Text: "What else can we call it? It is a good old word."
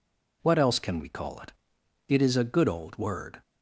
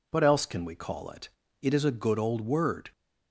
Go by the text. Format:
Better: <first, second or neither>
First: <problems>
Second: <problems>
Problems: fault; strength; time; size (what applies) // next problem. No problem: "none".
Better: neither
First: none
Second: none